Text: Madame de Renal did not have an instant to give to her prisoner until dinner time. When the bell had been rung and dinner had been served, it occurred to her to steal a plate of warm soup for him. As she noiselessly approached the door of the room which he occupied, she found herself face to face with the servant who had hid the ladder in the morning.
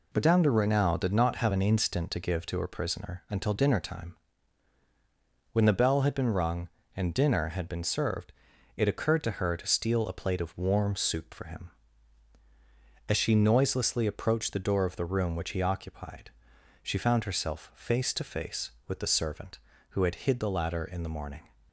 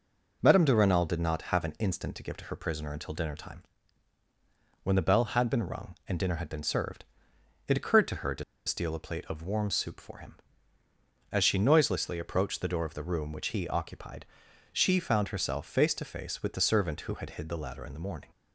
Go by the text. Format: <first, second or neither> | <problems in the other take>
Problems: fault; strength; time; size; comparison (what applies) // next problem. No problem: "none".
first | pauses between "to" and "steal"; slight; at 8.4 s; 0.24 s long